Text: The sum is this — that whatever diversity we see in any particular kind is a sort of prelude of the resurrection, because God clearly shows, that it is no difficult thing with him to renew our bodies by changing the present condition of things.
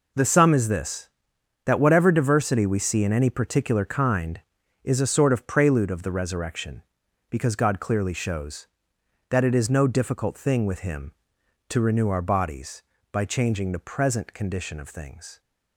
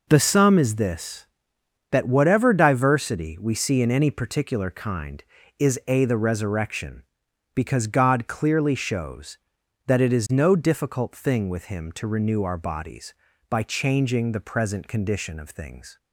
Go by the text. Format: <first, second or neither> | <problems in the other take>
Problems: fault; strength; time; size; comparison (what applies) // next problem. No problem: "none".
first | skips "sort of prelude of"; at 6.0 s